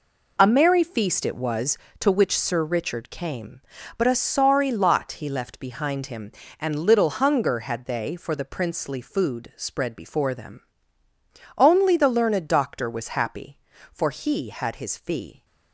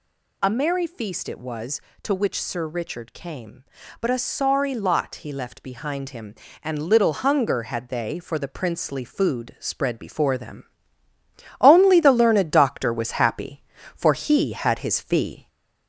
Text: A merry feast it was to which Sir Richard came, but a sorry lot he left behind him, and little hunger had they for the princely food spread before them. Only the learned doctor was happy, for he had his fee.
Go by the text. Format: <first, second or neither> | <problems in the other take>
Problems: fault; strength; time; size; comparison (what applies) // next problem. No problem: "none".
first | gets louder; slight; throughout; 2.5 dB